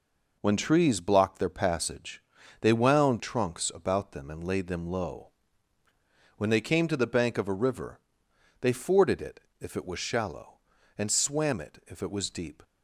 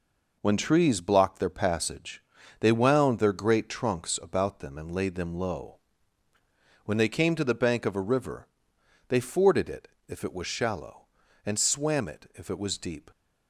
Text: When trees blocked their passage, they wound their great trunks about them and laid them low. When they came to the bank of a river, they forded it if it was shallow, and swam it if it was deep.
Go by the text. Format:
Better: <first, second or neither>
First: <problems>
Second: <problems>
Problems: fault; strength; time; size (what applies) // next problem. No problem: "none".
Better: second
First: skips "their great"; at 3.2 s // pauses between "it" and "if"; slight; at 9.3 s; 0.20 s long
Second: pauses between "it" and "if"; slight; at 9.8 s; 0.20 s long